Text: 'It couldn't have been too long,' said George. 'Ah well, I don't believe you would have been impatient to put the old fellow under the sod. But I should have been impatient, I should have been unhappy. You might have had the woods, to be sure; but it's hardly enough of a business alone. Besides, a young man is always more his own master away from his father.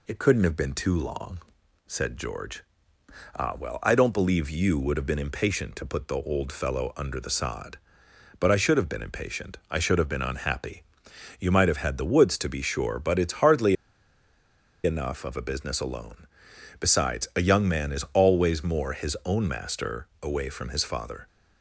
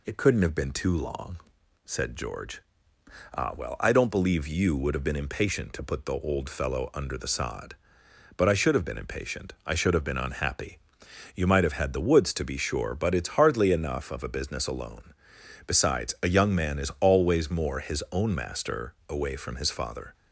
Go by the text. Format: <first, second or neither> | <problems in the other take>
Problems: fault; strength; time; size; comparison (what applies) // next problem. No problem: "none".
second | pauses between "hardly" and "enough"; at 13.7 s; 1.0 s long // pauses between "master" and "away"; slight; at 20.0 s; 0.16 s long; slight in the second